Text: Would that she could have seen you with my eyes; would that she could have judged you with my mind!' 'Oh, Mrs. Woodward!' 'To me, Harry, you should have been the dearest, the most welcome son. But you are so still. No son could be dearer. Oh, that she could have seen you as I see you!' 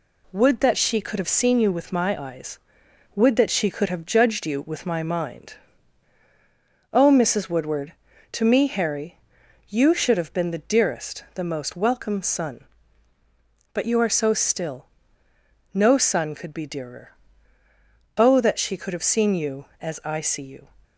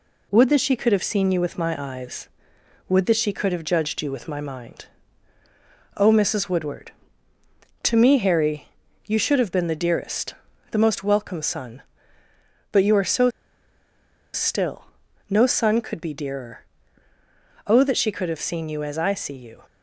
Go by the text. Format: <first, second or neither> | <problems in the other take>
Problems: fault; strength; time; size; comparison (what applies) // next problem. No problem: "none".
first | pauses between "so" and "still"; at 13.3 s; 1.0 s long